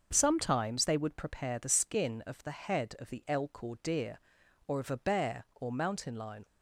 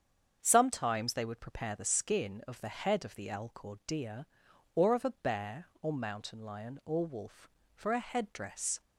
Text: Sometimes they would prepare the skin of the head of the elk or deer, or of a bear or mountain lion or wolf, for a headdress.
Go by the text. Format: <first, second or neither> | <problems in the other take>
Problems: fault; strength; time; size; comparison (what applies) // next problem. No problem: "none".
second | starts louder than the rest; until 1.1 s; 6.5 dB; strong in the second // stops before "or wolf for a headdress"; at 6.4 s